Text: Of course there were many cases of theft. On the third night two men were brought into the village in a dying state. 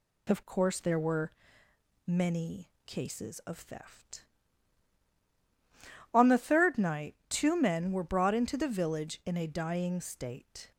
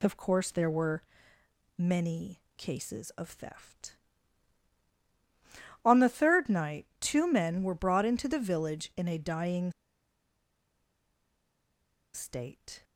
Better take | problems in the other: first | pauses between "were" and "many"; noticeable; at 1.0 s; 0.76 s long; noticeable in the first // pauses between "many" and "cases"; slight; at 2.4 s; 0.16 s long; slight in the first // pauses between "dying" and "state"; strong; at 9.7 s; 2.4 s long

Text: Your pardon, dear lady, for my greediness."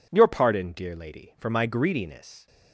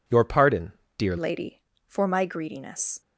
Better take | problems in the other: first | changes voice at "lady"; from 1.1 s on; 1.9 s long

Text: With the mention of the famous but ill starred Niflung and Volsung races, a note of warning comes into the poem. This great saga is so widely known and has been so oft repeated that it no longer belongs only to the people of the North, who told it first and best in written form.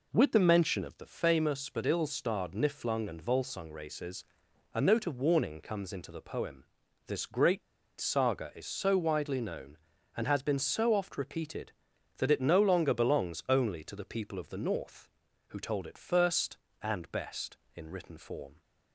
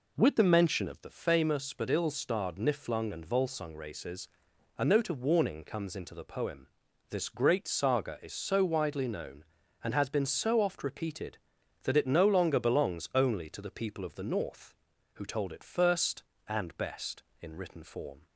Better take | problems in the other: second | pauses between "great" and "saga"; at 7.6 s; 0.38 s long

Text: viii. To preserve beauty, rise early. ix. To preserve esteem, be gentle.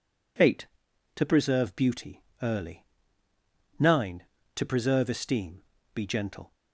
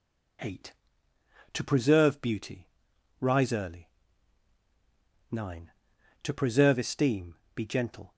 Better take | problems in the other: second | skips "rise"; at 2.3 s

